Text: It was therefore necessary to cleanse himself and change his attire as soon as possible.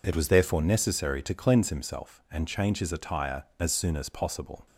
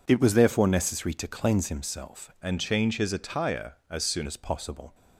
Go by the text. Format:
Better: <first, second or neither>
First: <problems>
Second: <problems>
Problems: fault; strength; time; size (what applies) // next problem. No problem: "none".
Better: first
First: none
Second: changes voice from "and" to "soon"; from 2.4 to 4.2 s; 1.8 s long